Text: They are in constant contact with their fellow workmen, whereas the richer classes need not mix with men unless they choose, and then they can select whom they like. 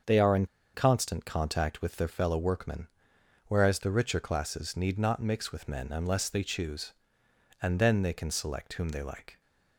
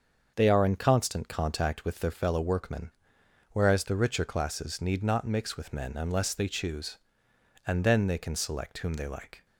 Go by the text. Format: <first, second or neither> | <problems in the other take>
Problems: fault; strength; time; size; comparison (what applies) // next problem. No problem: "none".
second | starts louder than the rest; until 1.3 s; 6.5 dB; also in the second // pauses between "in" and "constant"; slight; at 0.4 s; 0.28 s long